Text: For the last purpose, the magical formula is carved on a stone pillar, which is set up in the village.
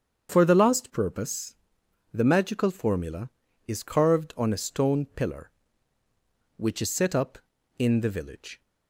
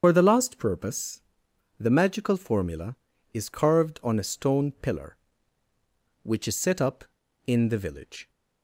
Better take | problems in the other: first | loses the start of "For"; at 0.0 s; 70 ms // starts louder than the rest; strong; until 1.0 s; 7 dB; strong in the first

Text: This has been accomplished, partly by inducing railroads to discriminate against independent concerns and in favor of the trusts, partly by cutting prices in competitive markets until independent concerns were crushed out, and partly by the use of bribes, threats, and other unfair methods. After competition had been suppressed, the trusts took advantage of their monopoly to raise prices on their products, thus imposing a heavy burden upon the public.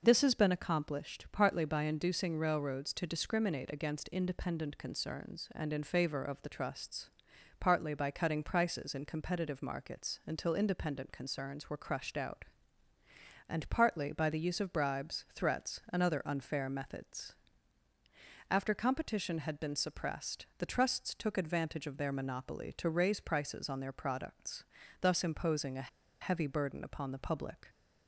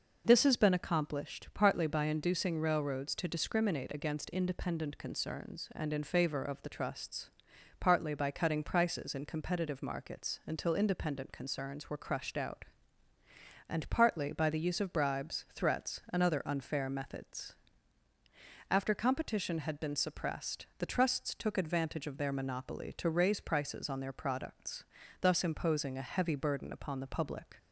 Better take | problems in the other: second | pauses between "a" and "heavy"; slight; at 25.8 s; 0.33 s long

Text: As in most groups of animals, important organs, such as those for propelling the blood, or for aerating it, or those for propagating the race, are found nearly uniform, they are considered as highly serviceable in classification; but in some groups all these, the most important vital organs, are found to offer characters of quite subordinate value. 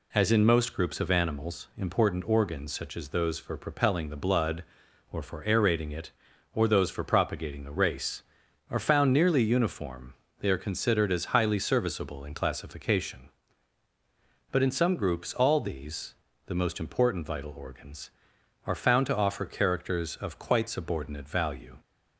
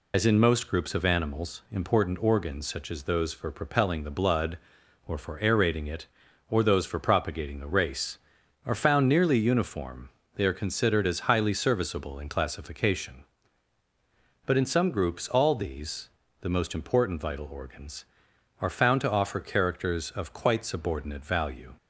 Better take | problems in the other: first | loses the start of "As"; at 0.1 s; 75 ms

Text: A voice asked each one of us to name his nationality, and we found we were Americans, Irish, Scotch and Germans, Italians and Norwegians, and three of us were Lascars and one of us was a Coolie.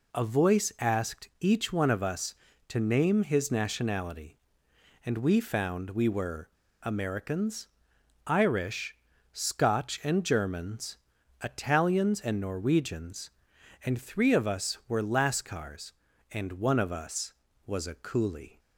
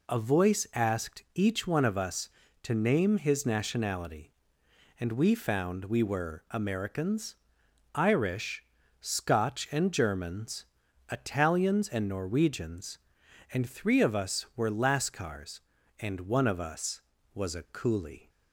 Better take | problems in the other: second | pauses between "were" and "Americans"; slight; at 6.4 s; 0.34 s long

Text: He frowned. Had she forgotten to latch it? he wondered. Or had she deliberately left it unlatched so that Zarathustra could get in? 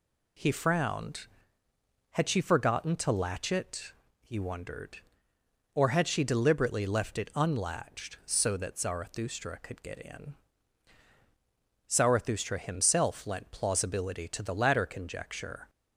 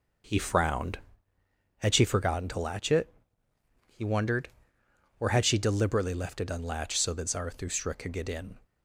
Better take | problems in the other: second | goes on to say "Zarathustra himself lent plausibility to the latter conjecture"; strong; from 11.8 s on; 3.8 s long

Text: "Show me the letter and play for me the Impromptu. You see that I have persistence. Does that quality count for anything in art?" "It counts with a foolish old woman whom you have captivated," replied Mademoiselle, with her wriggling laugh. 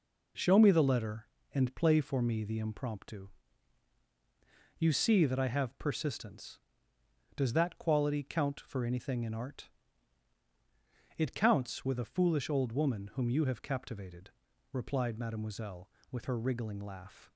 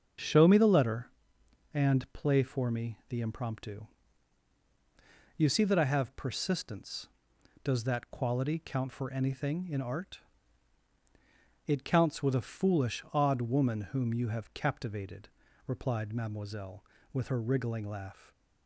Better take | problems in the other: first | starts louder than the rest; until 1.8 s; 7 dB // says "odd" for "old"; at 13.1 s

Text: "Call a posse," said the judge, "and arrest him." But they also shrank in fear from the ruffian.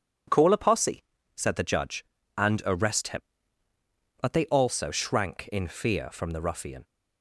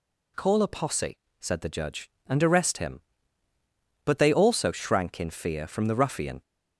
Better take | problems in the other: neither | none

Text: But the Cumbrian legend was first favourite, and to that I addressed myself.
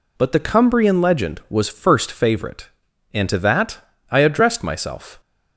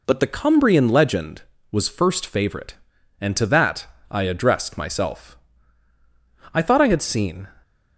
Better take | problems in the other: first | pauses between "that" and "I"; slight; at 3.8 s; 0.24 s long; slight in the first // goes on to say "I thought I had seen"; noticeable; from 6.5 s on; 0.94 s long

